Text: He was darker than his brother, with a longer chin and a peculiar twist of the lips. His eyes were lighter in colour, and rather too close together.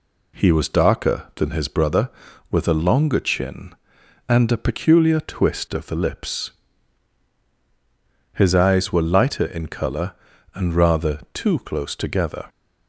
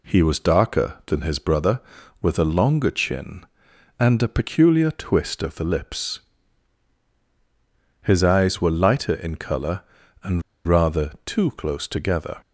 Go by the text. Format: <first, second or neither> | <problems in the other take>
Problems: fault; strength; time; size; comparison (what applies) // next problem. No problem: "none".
first | pauses between "and" and "rather"; slight; at 10.4 s; 0.24 s long